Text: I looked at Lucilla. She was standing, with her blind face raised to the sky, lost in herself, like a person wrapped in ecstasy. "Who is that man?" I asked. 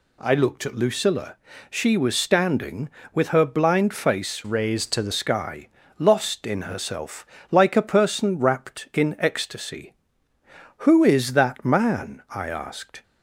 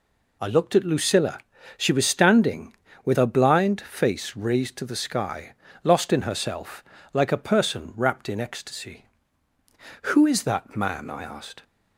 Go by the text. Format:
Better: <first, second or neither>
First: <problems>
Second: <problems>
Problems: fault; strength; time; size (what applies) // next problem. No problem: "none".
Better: second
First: changes voice from "raised" to "the"; from 4.4 to 5.1 s; 0.7 s long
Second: none